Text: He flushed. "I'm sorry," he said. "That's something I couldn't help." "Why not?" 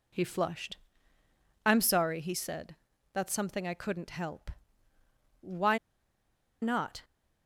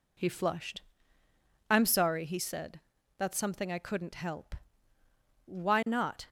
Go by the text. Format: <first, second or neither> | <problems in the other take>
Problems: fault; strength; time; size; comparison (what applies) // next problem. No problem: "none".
second | pauses between "Why" and "not"; noticeable; at 5.7 s; 0.84 s long